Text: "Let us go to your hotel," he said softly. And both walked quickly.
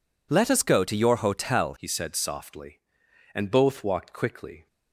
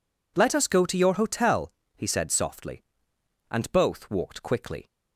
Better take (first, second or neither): second